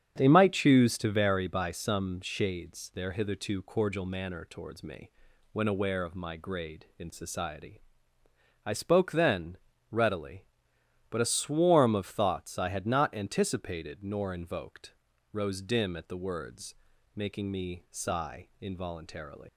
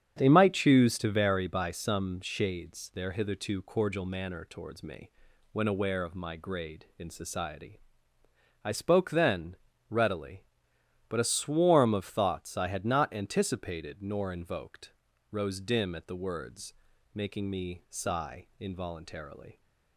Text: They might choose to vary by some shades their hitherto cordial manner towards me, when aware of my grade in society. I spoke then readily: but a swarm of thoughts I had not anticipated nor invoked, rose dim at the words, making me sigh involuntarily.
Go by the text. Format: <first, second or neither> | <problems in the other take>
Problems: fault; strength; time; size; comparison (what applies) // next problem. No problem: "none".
second | starts louder than the rest; strong; until 1.1 s; 8.5 dB; strong in the second // pauses between "then" and "readily"; slight; at 9.5 s; 0.34 s long; slight in the second // leaves "involuntarily" unfinished; at 19.4 s; 130 ms